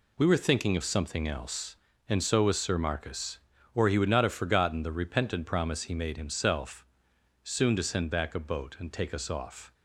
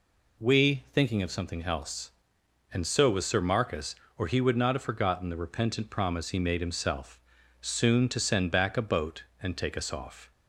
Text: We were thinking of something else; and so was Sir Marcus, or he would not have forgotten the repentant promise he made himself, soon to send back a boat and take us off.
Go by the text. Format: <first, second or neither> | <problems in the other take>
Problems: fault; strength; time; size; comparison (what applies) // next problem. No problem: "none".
first | skips "were"; at 0.8 s